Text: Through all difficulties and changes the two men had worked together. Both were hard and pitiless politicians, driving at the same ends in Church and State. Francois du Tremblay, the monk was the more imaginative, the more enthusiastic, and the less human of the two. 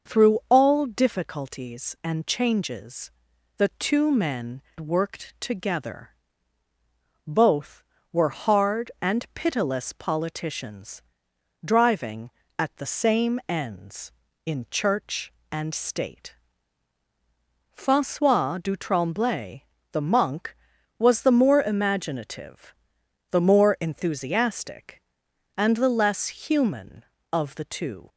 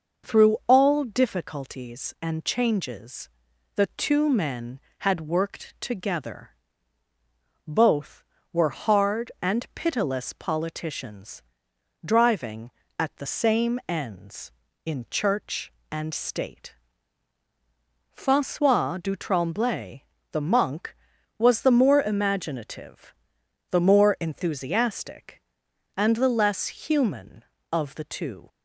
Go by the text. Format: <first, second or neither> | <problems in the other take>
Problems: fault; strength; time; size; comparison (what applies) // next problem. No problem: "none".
second | starts louder than the rest; noticeable; until 1.1 s; 6 dB // pauses between "changes" and "the"; noticeable; at 3.1 s; 0.46 s long; noticeable in the second // skips "had"; at 4.7 s